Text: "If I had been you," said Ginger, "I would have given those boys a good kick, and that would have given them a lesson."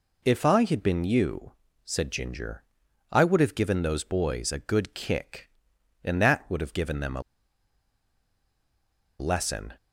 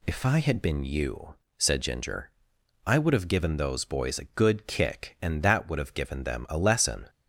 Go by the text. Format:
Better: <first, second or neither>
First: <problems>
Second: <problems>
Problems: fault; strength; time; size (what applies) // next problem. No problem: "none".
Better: second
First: pauses between "a" and "lesson"; strong; at 7.2 s; 1.9 s long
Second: none